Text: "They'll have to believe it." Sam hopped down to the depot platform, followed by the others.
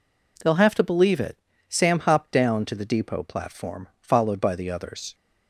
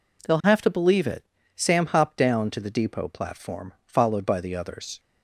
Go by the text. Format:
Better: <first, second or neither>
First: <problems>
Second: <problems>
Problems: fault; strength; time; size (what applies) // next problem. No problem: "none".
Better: neither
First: none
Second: none